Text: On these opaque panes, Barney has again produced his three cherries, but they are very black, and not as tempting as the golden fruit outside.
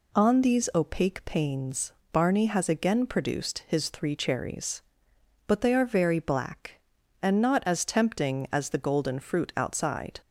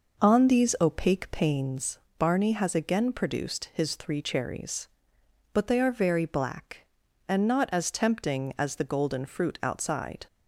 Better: first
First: none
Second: starts louder than the rest; noticeable; until 1.9 s; 5.5 dB

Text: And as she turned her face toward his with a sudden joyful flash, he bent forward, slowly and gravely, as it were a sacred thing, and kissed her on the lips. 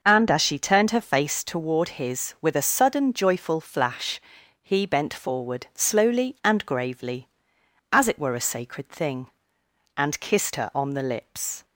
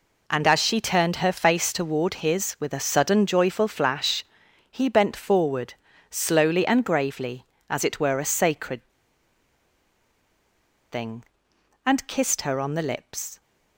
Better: first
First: none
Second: pauses between "sacred" and "thing"; strong; at 8.8 s; 2.0 s long

